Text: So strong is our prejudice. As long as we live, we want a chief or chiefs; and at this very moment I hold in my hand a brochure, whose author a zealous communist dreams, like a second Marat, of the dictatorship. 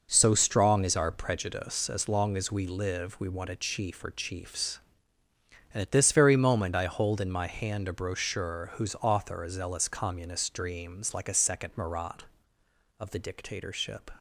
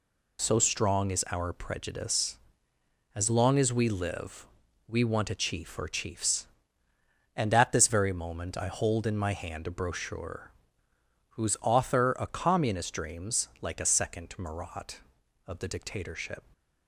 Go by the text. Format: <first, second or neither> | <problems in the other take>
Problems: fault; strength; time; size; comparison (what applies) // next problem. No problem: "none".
first | skips "zealous"; at 12.2 s